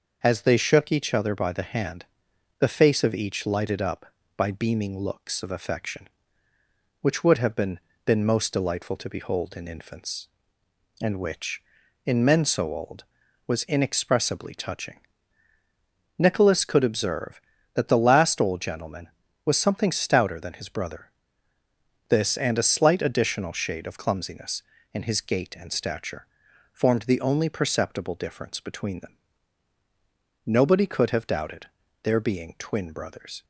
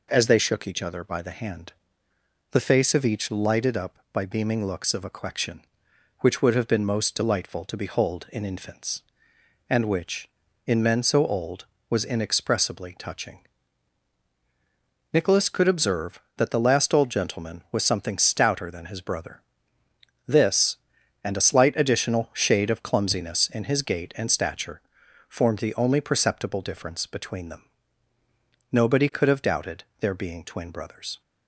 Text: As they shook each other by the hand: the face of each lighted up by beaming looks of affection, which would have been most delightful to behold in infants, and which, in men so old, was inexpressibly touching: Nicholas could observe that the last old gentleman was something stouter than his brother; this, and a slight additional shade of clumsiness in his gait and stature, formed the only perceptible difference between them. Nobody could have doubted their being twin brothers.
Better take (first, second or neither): second